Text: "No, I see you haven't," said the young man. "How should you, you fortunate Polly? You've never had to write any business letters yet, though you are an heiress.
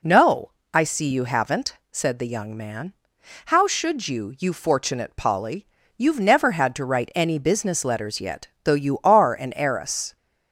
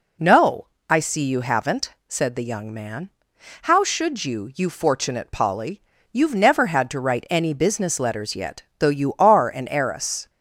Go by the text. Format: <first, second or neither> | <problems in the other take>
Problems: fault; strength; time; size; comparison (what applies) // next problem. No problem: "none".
neither | none